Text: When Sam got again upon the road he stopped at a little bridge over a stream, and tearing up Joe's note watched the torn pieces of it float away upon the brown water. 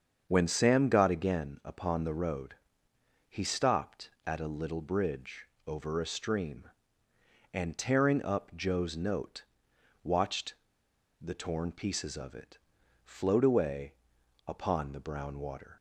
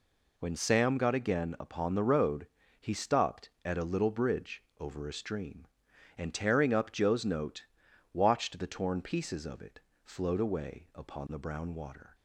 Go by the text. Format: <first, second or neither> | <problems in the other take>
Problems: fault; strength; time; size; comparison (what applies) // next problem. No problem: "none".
second | starts louder than the rest; until 1.3 s; 7 dB // pauses between "road" and "he"; noticeable; at 2.5 s; 0.74 s long; slight in the second // pauses between "bridge" and "over"; slight; at 5.4 s; 0.20 s long; slight in the second // pauses between "note" and "watched"; noticeable; at 9.4 s; 0.60 s long; noticeable in the second // pauses between "watched" and "the"; noticeable; at 10.5 s; 0.64 s long // pauses between "it" and "float"; noticeable; at 12.5 s; 0.48 s long; slight in the second // pauses between "away" and "upon"; noticeable; at 13.9 s; 0.54 s long